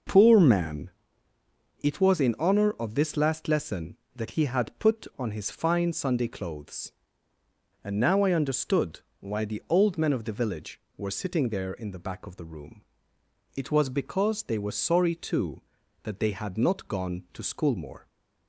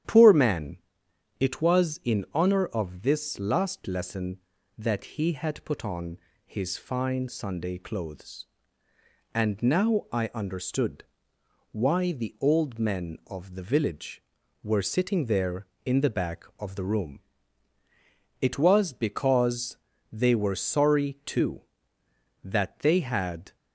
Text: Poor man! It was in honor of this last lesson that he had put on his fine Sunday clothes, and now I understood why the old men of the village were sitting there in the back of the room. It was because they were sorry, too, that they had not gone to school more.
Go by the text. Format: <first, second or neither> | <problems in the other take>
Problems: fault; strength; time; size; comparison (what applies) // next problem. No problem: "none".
first | starts louder than the rest; strong; until 1.6 s; 10.5 dB // pauses between "on" and "his"; slight; at 6.1 s; 0.26 s long // pauses between "understood" and "why"; noticeable; at 11.0 s; 0.68 s long; slight in the first // pauses between "because" and "they"; slight; at 19.7 s; 0.36 s long // stops before "not gone to school more"; at 23.5 s